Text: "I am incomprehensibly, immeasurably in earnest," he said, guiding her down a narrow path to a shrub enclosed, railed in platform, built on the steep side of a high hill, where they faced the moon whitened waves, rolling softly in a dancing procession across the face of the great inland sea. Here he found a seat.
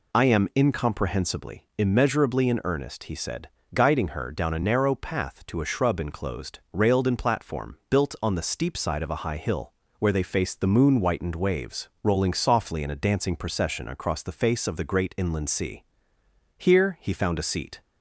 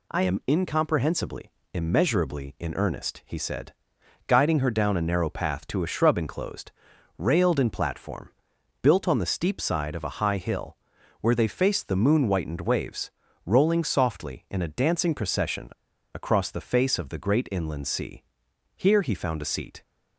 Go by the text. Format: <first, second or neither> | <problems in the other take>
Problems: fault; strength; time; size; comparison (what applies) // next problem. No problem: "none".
first | pauses between "procession" and "across"; at 15.7 s; 0.43 s long